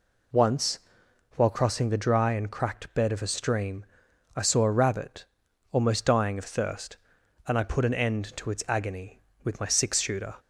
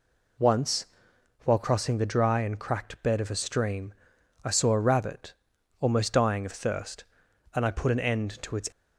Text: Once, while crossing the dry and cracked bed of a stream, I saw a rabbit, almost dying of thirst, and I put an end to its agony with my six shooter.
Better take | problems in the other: first | stops before "agony with my six shooter"; at 8.7 s

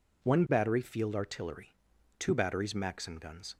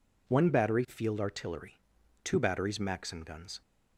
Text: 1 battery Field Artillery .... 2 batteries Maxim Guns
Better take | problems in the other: neither | none

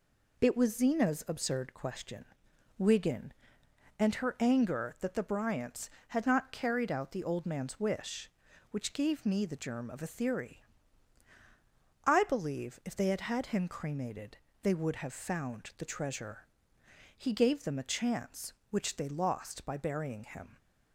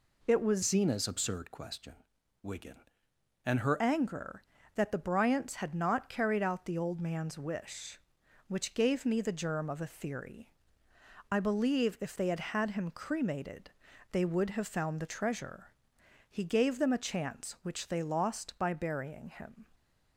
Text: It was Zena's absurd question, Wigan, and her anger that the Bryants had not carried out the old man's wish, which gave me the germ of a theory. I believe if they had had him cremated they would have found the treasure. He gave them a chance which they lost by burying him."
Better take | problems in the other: first | changes voice from "Zena's" to "her"; from 0.6 to 3.8 s; 3.2 s long // pauses between "cremated" and "they"; at 13.7 s; 0.42 s long; slight in the first

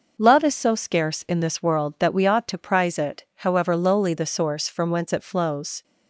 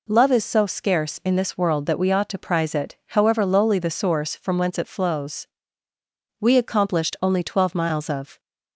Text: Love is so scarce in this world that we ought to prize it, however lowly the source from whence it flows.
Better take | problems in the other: first | goes on to say "We accomplished only twelve miles of"; strong; from 6.3 s on; 2.0 s long

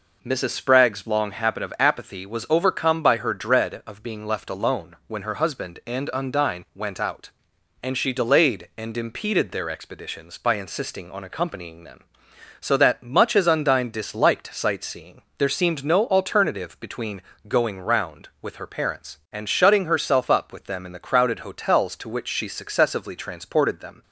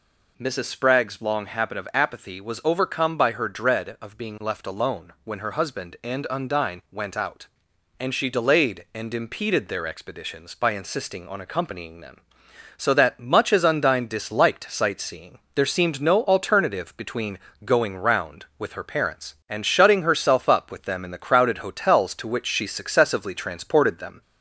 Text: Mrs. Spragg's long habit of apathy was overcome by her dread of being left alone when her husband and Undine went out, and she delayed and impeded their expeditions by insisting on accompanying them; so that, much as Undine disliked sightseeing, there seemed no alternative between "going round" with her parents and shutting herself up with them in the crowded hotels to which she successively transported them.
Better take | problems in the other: first | gets louder; slight; throughout; 2 dB // pauses between "between" and "going"; slight; at 17.3 s; 0.26 s long; slight in the first

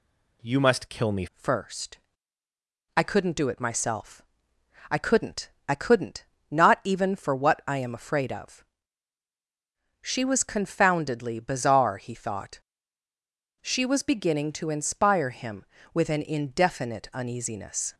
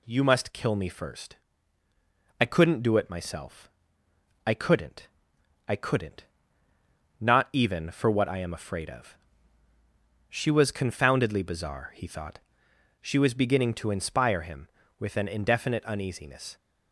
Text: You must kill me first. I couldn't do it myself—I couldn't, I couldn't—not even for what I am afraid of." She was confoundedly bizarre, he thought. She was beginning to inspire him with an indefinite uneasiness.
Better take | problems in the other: second | changes voice at "first"; from 1.3 s on; 16.6 s long

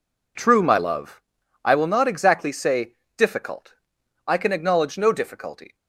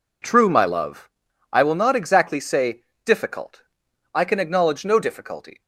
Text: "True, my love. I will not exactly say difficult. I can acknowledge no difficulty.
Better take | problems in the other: neither | pauses between "say" and "difficult"; slight; the same in both

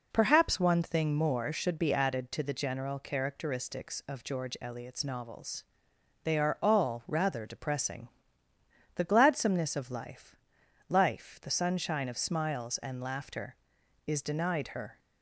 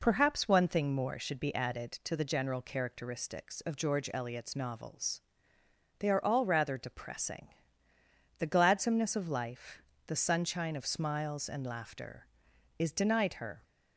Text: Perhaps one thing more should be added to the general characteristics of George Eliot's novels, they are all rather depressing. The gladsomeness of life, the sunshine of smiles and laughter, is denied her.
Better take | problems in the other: second | says "life" twice; at 10.8 s

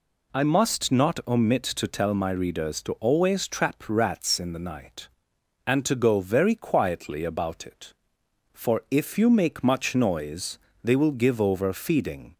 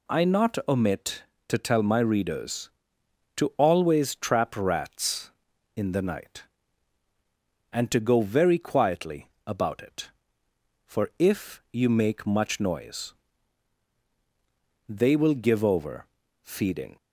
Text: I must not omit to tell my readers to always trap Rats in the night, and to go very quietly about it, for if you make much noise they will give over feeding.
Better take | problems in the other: first | skips "must"; at 0.2 s // pauses between "quietly" and "about"; slight; at 9.2 s; 0.20 s long // pauses between "noise" and "they"; strong; at 13.1 s; 1.7 s long; slight in the first // pauses between "over" and "feeding"; slight; at 16.0 s; 0.34 s long

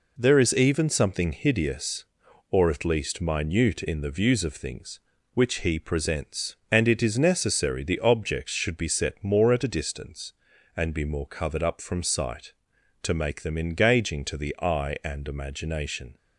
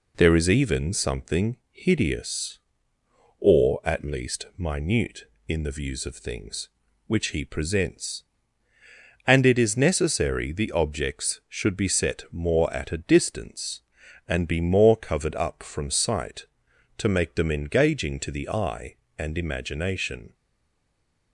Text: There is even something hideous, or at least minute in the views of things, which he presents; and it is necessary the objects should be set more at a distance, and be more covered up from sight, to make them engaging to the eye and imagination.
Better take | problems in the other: first | stays silent after the last word; from 20.3 s on; 1.0 s long

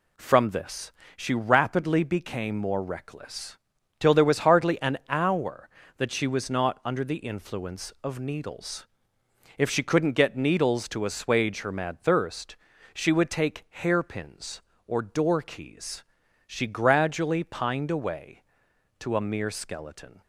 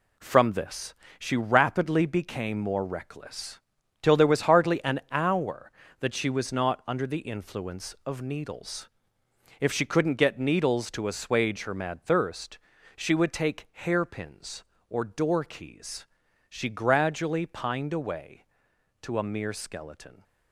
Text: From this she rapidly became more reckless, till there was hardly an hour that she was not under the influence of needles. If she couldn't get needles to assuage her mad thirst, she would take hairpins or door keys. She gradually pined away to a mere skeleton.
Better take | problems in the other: first | gets quieter; strong; throughout; 7.5 dB // pauses between "this" and "she"; slight; at 0.9 s; 0.26 s long; slight in the first

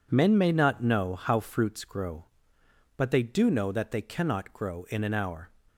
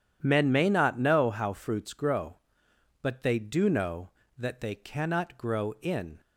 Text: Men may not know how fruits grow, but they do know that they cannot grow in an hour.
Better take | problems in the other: first | stops before "an hour"; at 6.1 s

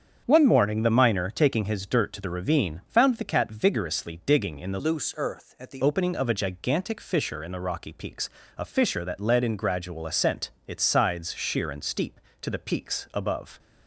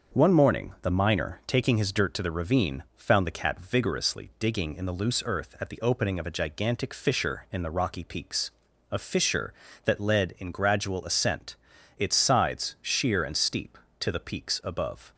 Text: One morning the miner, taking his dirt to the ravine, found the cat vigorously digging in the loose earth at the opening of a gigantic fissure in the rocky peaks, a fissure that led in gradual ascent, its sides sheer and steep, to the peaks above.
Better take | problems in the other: second | starts louder than the rest; strong; until 1.2 s; 7.5 dB; also in the second // changes voice from "loose" to "the"; from 4.7 to 5.8 s; 1.1 s long

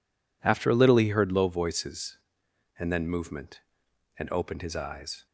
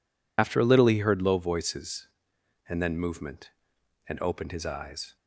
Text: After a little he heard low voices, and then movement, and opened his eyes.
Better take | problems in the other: first | loses the start of "After"; at 0.3 s; 65 ms

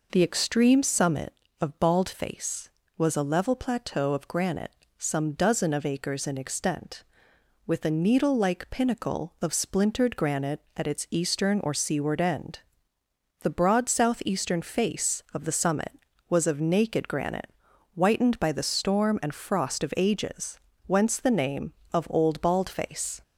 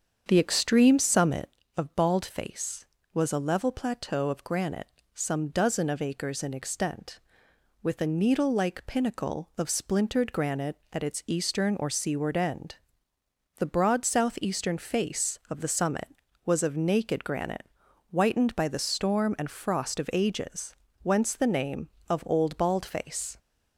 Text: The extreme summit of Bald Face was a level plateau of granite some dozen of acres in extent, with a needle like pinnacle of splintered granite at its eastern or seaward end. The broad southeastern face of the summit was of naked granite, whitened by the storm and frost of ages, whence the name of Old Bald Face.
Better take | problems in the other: first | starts louder than the rest; strong; until 1.7 s; 7.5 dB // pauses between "granite" and "some"; slight; at 4.8 s; 0.26 s long; slight in the first

